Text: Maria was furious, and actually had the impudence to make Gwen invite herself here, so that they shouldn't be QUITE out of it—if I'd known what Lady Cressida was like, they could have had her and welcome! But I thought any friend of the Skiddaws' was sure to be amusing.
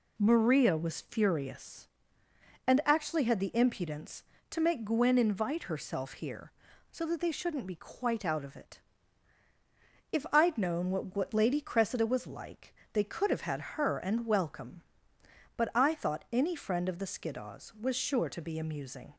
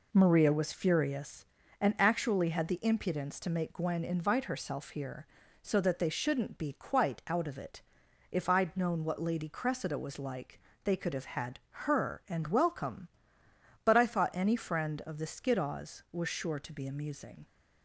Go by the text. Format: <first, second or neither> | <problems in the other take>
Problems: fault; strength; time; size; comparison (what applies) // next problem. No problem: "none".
second | says "what" twice; at 11.1 s